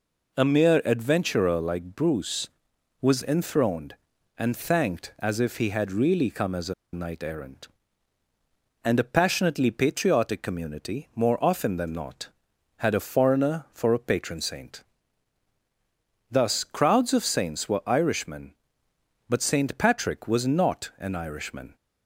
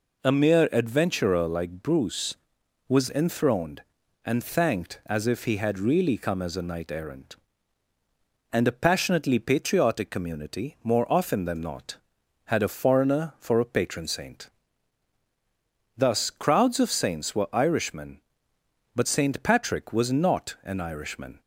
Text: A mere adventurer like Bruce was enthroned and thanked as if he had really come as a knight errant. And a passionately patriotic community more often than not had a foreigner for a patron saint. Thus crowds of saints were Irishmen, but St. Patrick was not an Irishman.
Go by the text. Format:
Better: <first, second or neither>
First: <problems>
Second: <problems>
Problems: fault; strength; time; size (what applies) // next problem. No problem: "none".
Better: second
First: pauses between "a" and "knight"; slight; at 6.7 s; 0.19 s long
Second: none